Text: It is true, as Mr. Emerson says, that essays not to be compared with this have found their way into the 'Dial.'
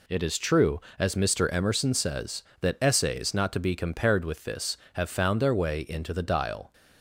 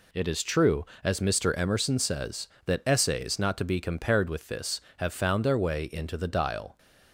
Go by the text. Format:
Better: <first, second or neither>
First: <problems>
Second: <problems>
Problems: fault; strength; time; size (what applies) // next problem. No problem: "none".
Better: neither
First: none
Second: none